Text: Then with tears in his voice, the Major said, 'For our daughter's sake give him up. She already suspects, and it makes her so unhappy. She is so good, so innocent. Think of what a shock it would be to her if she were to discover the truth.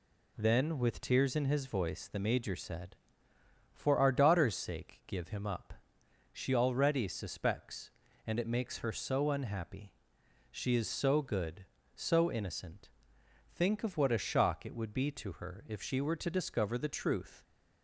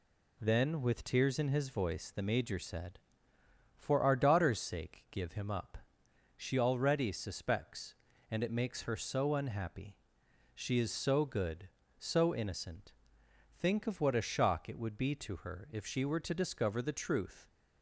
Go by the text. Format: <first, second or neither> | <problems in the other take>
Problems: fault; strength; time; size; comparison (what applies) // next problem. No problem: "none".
neither | none